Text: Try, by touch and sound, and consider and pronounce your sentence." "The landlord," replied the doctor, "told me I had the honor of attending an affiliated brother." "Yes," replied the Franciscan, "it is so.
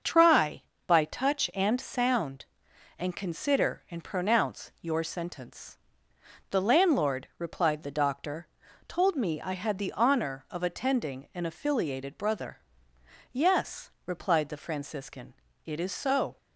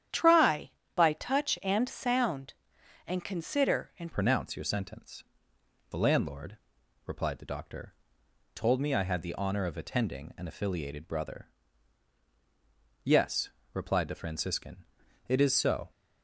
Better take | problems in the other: first | starts louder than the rest; strong; until 1.3 s; 10 dB; also in the first // changes voice at "pronounce"; from 4.1 s on; 11.8 s long

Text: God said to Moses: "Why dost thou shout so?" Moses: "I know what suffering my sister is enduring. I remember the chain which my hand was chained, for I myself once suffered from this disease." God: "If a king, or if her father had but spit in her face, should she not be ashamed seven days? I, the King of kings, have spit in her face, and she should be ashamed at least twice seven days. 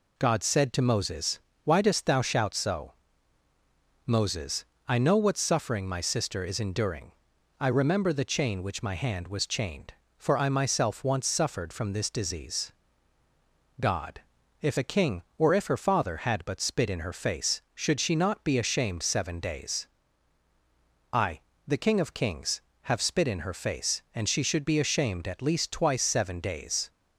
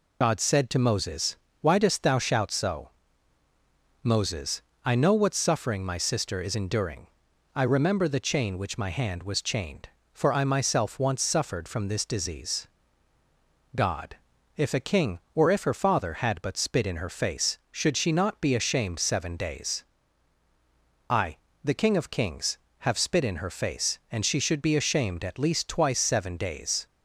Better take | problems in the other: first | loses the start of "God"; at 0.2 s; 55 ms

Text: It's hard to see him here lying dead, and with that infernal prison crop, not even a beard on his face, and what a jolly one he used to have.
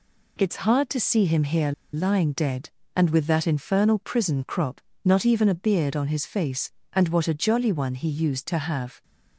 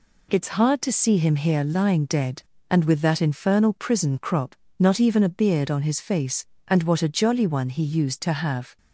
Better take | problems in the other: second | pauses between "here" and "lying"; slight; at 1.7 s; 0.21 s long

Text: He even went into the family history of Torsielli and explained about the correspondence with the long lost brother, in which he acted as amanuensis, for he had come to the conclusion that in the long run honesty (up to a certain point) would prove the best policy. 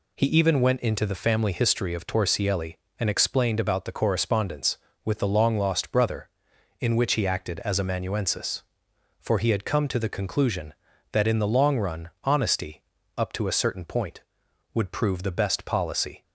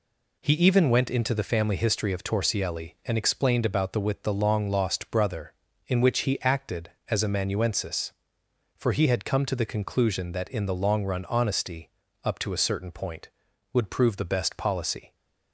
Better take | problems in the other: first | skips "correspondence"; at 4.0 s

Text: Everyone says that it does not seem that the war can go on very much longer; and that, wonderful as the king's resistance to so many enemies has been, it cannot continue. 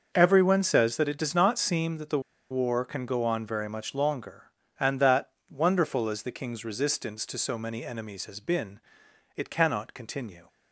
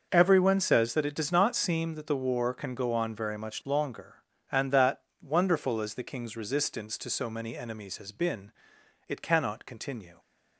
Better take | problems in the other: second | starts louder than the rest; until 1.1 s; 6.5 dB; also in the second // pauses between "the" and "war"; slight; at 2.1 s; 0.31 s long

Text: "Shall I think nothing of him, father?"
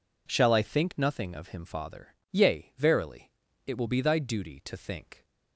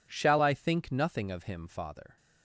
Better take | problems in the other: second | goes on to say "Yea verily it will be thy duty to think"; strong; from 2.3 s on; 2.9 s long

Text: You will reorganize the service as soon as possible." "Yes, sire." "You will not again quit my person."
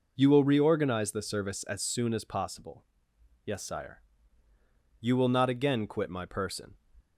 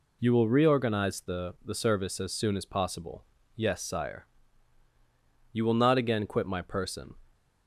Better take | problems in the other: first | says "the" twice; at 1.6 s

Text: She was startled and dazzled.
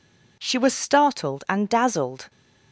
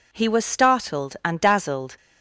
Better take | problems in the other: first | says "He" for "She"; at 0.1 s

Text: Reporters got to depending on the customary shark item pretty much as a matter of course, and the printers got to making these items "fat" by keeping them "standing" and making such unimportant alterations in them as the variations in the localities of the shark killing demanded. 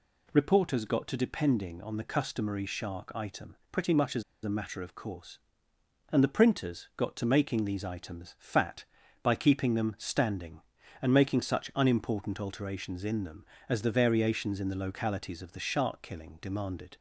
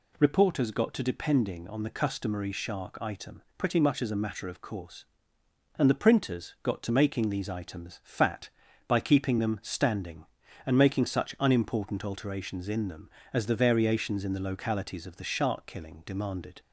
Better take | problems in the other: second | pauses between "item" and "pretty"; slight; at 3.5 s; 0.16 s long; slight in the second // pauses between "as" and "a"; slight; at 4.2 s; 0.22 s long

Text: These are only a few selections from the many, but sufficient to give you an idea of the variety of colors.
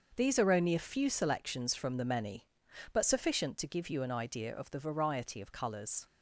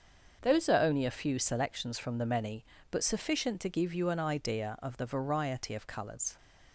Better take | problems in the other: first | starts louder than the rest; until 1.4 s; 6.5 dB; also in the first // says "Those" for "These"; at 0.4 s

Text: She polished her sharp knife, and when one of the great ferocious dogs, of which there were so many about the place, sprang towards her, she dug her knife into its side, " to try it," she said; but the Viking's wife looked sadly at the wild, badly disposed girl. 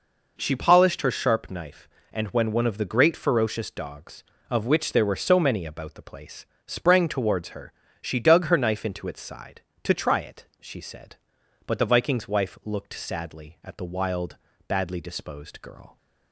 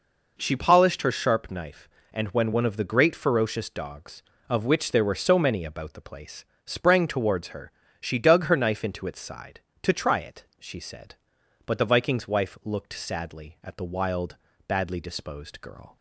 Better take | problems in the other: neither | none

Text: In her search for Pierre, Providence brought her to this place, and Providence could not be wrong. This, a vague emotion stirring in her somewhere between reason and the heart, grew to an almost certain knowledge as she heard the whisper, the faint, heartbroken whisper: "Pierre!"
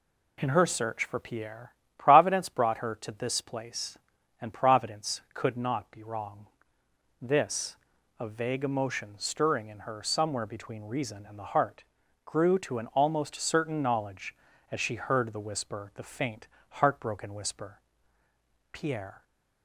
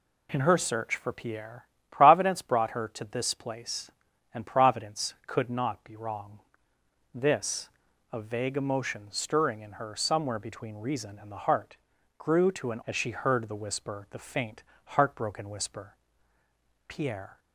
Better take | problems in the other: first | skips "almost certain knowledge"; at 12.8 s

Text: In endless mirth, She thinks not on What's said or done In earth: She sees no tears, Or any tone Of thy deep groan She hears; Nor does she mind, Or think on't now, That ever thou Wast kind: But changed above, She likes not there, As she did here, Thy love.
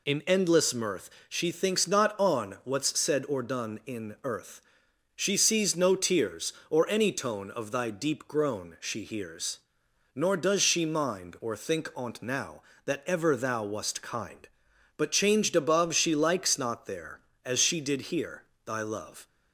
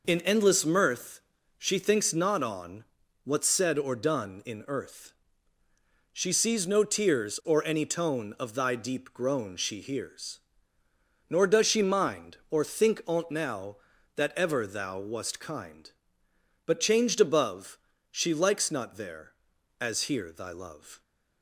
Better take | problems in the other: first | pauses between "on" and "What's"; at 2.8 s; 0.40 s long // skips "she did"; at 20.0 s

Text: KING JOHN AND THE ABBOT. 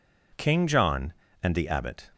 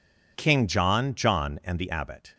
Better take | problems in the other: first | says "JOHN" twice; at 1.1 s

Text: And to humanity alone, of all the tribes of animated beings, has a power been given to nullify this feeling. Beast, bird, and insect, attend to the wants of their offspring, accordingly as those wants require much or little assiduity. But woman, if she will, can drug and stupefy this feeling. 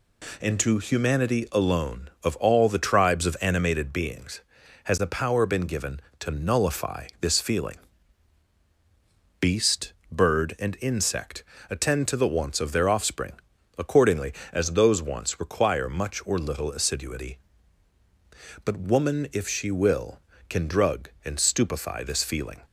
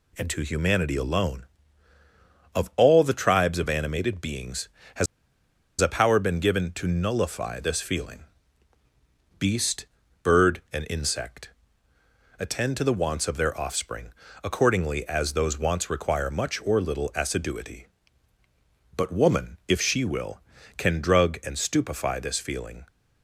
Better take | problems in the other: first | pauses between "has" and "a"; noticeable; at 5.0 s; 0.74 s long

